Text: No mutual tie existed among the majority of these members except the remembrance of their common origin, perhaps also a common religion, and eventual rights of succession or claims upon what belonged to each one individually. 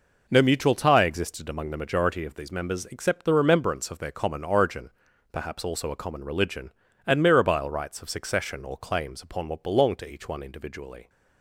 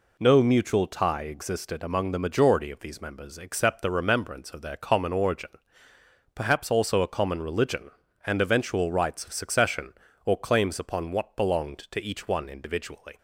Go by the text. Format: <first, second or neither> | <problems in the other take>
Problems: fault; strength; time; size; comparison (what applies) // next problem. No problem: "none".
second | says "mirabile" for "eventual"; at 7.2 s